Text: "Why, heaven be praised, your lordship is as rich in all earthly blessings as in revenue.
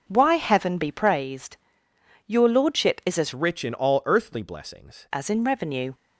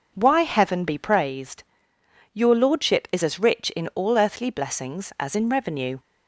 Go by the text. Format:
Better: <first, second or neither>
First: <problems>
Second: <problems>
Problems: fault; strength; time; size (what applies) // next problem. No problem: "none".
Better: second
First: starts louder than the rest; noticeable; until 1.0 s; 6 dB // changes voice from "rich" to "blessings"; from 3.3 to 5.0 s; 1.7 s long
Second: none